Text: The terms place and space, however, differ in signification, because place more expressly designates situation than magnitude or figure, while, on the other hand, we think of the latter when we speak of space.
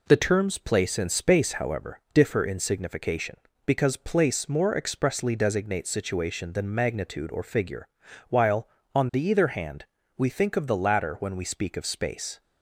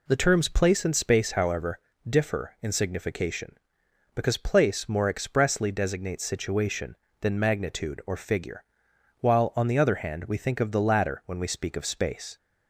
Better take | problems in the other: second | says "either" for "other"; at 9.2 s

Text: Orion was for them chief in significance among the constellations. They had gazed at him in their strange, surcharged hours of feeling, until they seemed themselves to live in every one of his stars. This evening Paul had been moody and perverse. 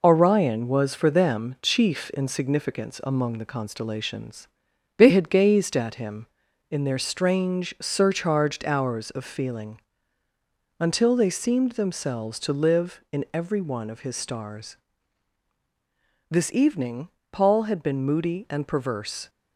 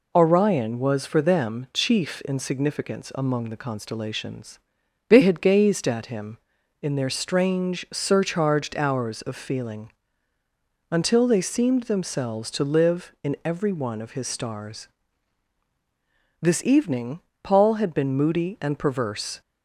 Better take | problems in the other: second | gets quieter; noticeable; throughout; 4.5 dB // pauses between "evening" and "Paul"; slight; at 17.0 s; 0.22 s long; slight in the second

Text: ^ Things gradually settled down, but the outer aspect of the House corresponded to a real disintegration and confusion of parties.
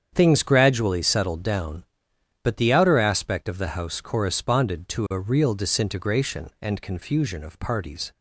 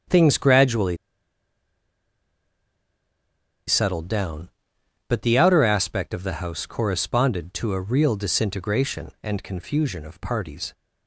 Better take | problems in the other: first | starts louder than the rest; strong; until 3.8 s; 8 dB; strong in the first // pauses between "gradually" and "settled"; strong; at 0.9 s; 2.7 s long

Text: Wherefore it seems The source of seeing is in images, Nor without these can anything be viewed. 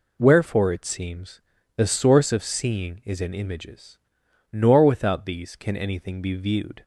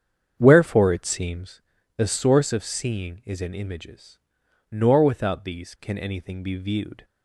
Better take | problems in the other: first | starts louder than the rest; strong; until 1.5 s; 8 dB // pauses between "seems" and "The"; slight; at 1.6 s; 0.34 s long; slight in the first

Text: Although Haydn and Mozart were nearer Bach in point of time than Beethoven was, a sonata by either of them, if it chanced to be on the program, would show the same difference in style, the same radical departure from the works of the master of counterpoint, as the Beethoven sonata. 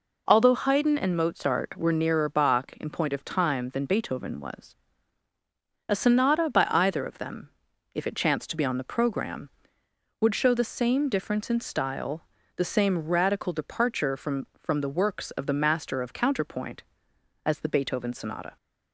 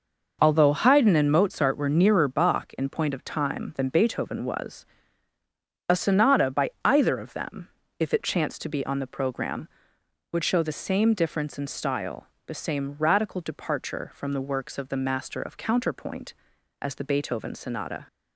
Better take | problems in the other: second | says "from" twice; at 14.5 s

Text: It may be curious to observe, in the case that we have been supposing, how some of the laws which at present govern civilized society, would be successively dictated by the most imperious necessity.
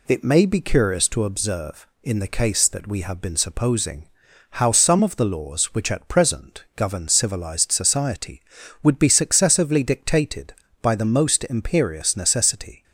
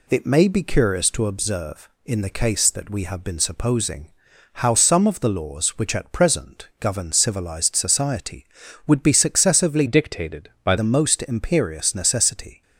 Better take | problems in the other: first | changes voice from "dictated" to "by"; from 9.8 to 10.7 s; 0.9 s long

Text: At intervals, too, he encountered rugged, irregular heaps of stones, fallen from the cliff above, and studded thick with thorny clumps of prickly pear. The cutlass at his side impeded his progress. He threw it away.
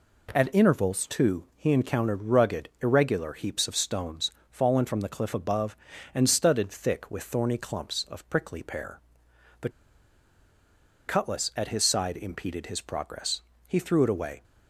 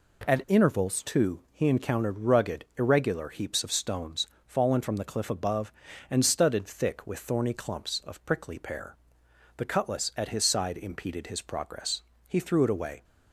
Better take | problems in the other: second | pauses between "The" and "cutlass"; strong; at 9.6 s; 1.3 s long

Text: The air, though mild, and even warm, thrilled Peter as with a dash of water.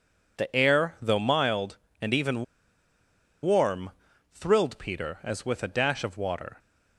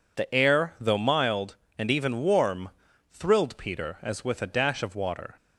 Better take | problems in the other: second | pauses between "even" and "warm"; at 2.4 s; 0.98 s long

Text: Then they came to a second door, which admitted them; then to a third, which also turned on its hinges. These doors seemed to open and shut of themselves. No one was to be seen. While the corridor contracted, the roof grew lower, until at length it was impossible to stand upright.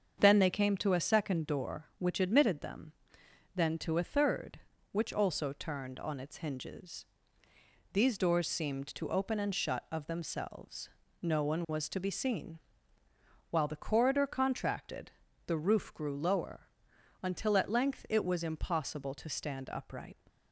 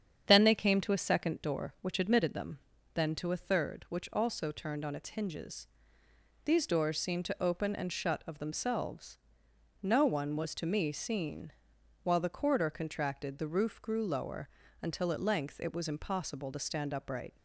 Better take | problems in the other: first | starts louder than the rest; strong; until 1.2 s; 8 dB; strong in the first // says "me" for "be"; at 10.6 s

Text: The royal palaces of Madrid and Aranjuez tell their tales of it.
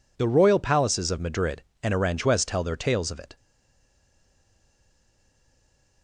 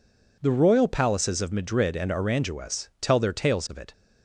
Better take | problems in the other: second | stays silent after the last word; strong; from 3.3 s on; 2.7 s long

